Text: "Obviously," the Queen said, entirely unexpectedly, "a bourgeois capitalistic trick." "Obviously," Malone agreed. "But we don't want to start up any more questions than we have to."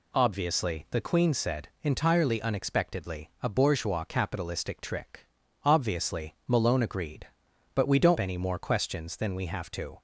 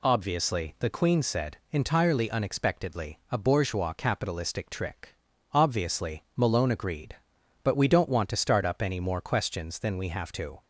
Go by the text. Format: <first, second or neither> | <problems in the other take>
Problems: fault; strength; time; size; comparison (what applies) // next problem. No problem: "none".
second | skips "want to start up"; at 8.1 s